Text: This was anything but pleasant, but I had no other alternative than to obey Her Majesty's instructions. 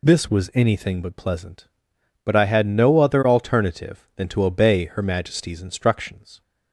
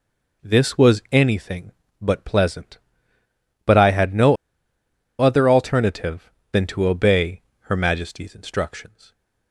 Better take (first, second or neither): first